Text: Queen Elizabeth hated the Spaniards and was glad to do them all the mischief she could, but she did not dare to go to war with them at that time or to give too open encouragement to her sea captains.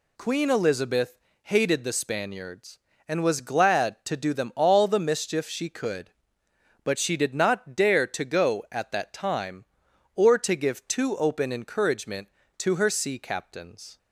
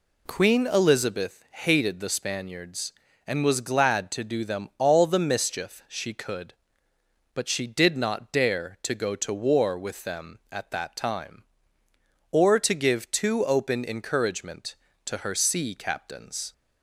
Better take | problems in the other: second | pauses between "Elizabeth" and "hated"; slight; at 1.1 s; 0.26 s long // skips "to war with them"; at 8.6 s

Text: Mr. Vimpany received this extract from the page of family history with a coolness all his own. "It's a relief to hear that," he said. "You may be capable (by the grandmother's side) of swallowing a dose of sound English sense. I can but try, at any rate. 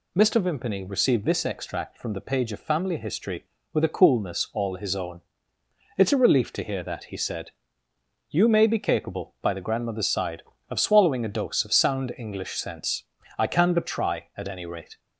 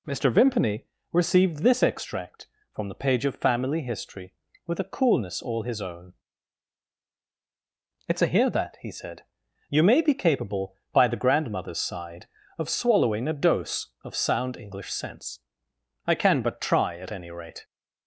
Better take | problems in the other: first | pauses between "Vimpany" and "received"; slight; at 0.8 s; 0.28 s long // skips "relief to"; at 8.2 s

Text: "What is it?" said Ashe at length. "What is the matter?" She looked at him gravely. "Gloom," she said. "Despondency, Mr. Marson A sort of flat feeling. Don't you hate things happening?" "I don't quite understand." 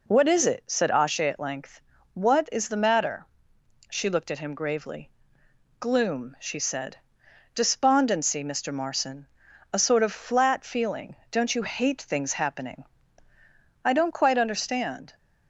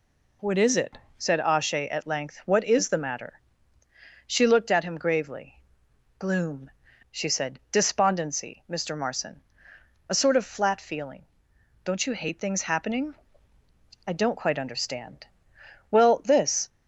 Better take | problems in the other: first | pauses between "Marson" and "A"; noticeable; at 9.4 s; 0.68 s long; noticeable in the first // goes on to say "Well this"; noticeable; from 15.8 s on; 0.80 s long

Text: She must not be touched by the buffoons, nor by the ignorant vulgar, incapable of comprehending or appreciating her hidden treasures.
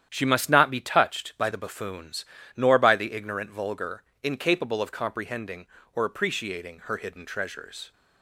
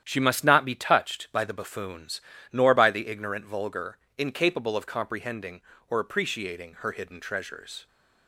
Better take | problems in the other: neither | starts louder than the rest; strong; the same in both

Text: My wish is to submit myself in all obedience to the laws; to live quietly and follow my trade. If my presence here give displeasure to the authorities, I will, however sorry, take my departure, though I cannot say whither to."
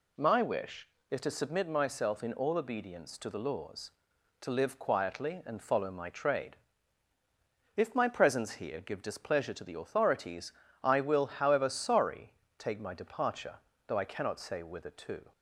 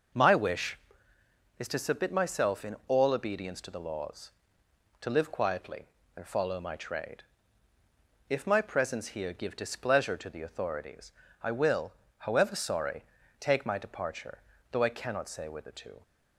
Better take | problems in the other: neither | none

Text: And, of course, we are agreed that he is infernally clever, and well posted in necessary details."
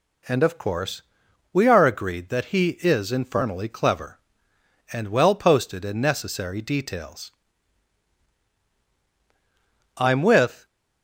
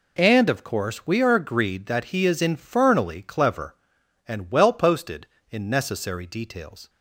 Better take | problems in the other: second | goes on to say "I'm with"; noticeable; from 9.9 s on; 0.68 s long

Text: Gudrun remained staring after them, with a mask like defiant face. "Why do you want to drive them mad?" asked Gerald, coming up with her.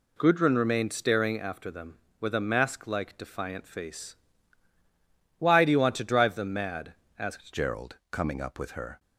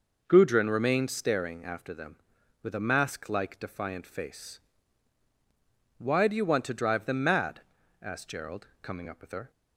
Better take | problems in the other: second | changes voice at "Gerald"; from 7.5 s on; 1.4 s long

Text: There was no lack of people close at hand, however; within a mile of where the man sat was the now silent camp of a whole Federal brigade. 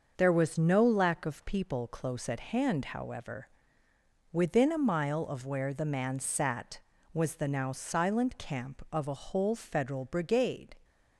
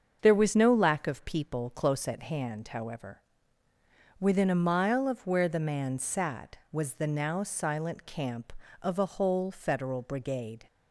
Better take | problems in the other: neither | starts louder than the rest; the same in both

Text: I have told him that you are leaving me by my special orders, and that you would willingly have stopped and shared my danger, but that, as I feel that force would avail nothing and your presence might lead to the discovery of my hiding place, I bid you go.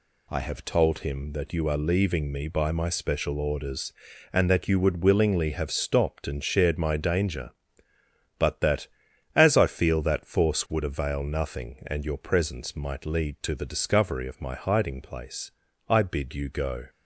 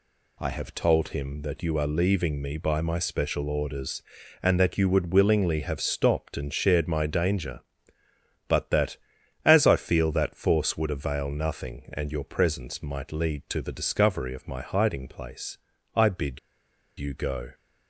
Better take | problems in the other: first | pauses between "bid" and "you"; noticeable; at 16.3 s; 0.60 s long

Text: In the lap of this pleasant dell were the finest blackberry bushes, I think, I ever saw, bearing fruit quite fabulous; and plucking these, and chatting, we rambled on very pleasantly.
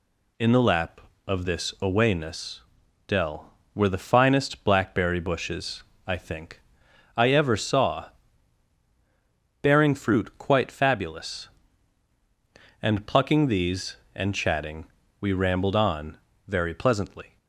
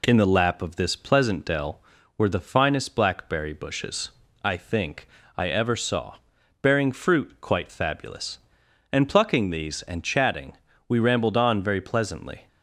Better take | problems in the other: second | says "awayness" for "pleasant"; at 1.7 s // pauses between "on" and "very"; slight; at 16.1 s; 0.30 s long

